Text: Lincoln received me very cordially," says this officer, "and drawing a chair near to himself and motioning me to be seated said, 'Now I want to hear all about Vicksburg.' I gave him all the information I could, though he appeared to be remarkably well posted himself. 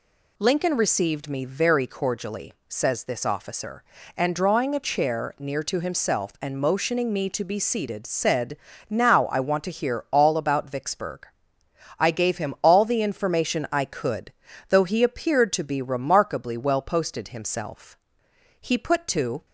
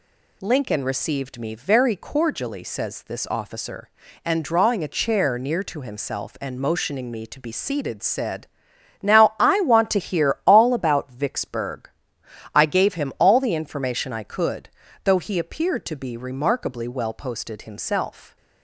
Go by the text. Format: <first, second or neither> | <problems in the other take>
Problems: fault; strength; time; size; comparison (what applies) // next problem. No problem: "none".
second | goes on to say "He put to"; noticeable; from 18.5 s on; 0.86 s long